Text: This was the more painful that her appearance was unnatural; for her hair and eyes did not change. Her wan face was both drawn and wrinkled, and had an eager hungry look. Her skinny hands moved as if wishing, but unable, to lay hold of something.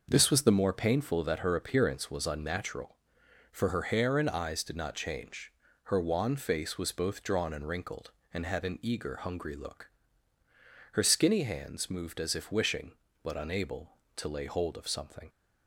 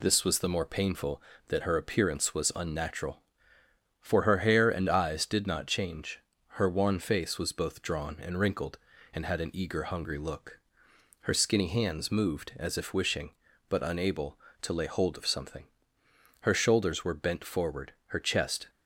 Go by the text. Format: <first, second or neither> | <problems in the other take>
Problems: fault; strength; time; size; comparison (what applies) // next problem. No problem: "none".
first | goes on to say "Her shoulders were bent forward her chest"; strong; from 16.3 s on; 2.3 s long